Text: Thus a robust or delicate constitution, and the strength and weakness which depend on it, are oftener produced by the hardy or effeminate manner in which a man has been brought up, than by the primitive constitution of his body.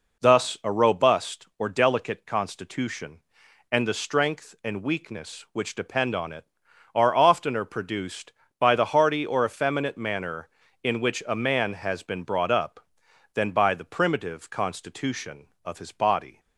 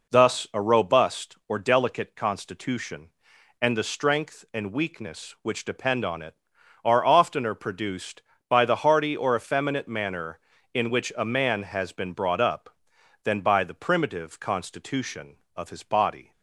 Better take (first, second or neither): neither